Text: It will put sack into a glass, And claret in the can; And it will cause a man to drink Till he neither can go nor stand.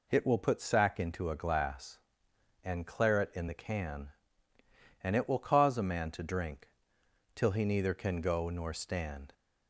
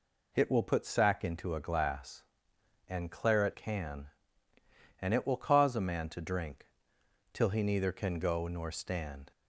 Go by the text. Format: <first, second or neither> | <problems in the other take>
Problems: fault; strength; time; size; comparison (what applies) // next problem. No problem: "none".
first | skips "in the"; at 3.5 s // pauses between "drink" and "Till"; noticeable; at 6.6 s; 0.66 s long; noticeable in the first